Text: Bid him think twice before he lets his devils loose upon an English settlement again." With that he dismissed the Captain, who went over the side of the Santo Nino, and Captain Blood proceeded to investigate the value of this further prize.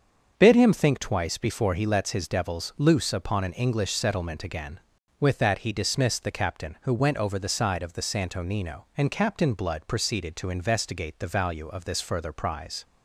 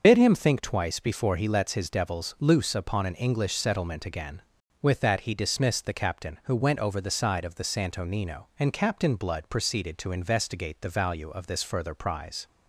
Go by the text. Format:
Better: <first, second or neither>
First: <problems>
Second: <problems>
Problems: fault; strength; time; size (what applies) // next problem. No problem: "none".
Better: first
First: starts louder than the rest; until 1.3 s; 7 dB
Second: loses the start of "Bid"; at 0.0 s; 60 ms // starts louder than the rest; until 1.0 s; 6.5 dB